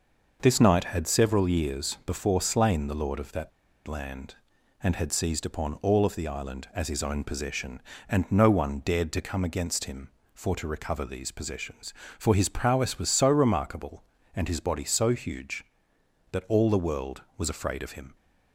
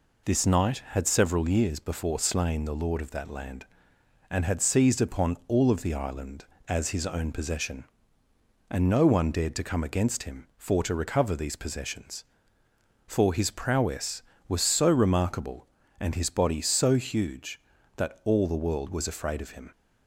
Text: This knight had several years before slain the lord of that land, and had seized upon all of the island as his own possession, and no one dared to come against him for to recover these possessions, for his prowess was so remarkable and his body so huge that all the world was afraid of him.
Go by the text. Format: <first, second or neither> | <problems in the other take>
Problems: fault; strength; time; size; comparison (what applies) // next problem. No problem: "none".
second | pauses between "that" and "land"; at 3.5 s; 0.36 s long